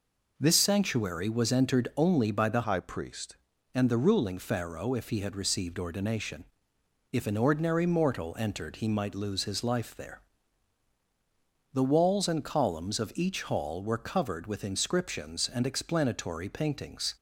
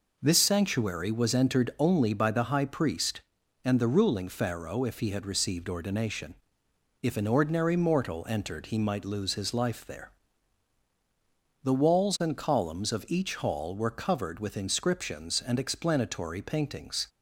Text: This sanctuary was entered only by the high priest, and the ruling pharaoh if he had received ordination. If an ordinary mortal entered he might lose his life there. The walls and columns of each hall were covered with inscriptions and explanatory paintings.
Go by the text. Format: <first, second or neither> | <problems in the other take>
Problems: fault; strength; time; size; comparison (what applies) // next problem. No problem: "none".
second | changes voice from "high" to "priest"; from 2.6 to 3.3 s; 0.7 s long